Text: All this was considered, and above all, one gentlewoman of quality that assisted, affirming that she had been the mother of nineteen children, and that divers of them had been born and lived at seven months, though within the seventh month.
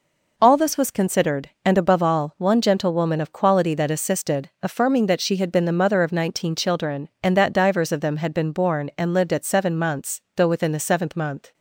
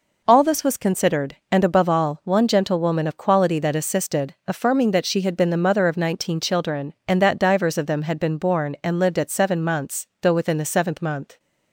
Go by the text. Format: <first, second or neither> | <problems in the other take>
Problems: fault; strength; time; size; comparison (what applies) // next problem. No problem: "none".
neither | none